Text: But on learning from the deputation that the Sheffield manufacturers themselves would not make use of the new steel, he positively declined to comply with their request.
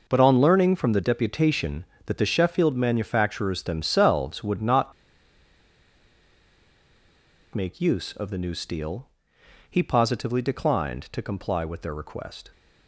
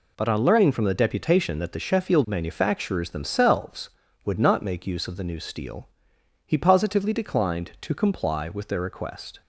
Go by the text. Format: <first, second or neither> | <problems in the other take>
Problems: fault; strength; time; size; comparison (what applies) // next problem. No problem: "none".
second | pauses between "not" and "make"; strong; at 4.9 s; 2.6 s long